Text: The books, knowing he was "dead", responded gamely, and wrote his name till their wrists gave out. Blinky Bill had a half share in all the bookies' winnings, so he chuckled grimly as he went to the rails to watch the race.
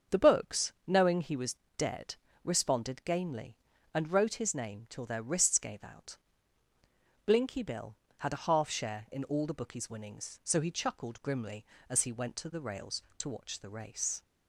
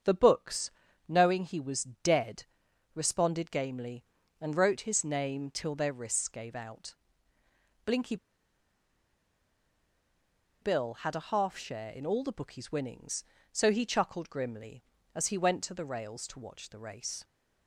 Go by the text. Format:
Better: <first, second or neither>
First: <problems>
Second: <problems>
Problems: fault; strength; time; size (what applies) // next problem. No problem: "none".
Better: first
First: starts louder than the rest; until 1.2 s; 7 dB // pauses between "was" and "dead"; slight; at 1.5 s; 0.20 s long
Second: starts louder than the rest; strong; until 1.4 s; 7.5 dB // pauses between "was" and "dead"; slight; at 1.8 s; 0.18 s long // pauses between "Blinky" and "Bill"; strong; at 8.1 s; 2.4 s long